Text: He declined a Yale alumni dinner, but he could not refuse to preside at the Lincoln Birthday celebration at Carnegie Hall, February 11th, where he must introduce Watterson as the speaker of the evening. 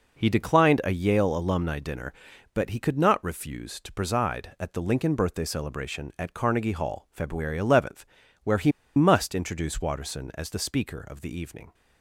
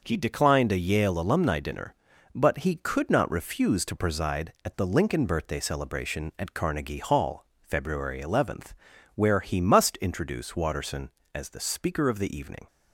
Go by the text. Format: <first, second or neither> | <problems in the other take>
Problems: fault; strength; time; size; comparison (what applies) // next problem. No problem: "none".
second | pauses between "he" and "must"; slight; at 8.7 s; 0.24 s long